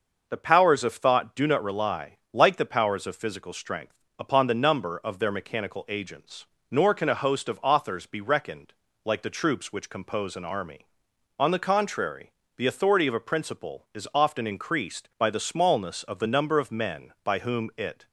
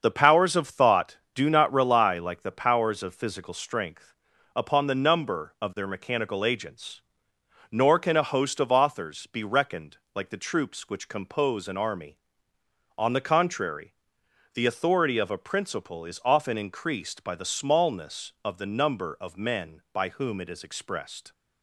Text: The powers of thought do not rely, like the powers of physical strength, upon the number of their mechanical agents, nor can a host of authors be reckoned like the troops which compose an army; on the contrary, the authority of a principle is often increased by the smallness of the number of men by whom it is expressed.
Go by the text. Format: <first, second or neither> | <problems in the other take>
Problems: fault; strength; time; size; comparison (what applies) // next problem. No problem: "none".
second | starts louder than the rest; noticeable; until 1.3 s; 6 dB; also in the second // pauses between "reckoned" and "like"; slight; at 8.7 s; 0.32 s long; slight in the second // stops before "is expressed"; at 18.0 s